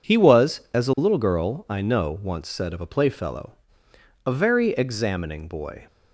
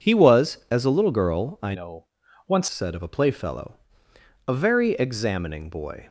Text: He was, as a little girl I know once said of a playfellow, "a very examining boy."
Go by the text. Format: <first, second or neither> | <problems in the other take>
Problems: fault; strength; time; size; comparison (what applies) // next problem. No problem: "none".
first | changes voice from "know" to "once"; from 1.7 to 2.6 s; 0.9 s long // pauses between "know" and "once"; at 2.0 s; 0.42 s long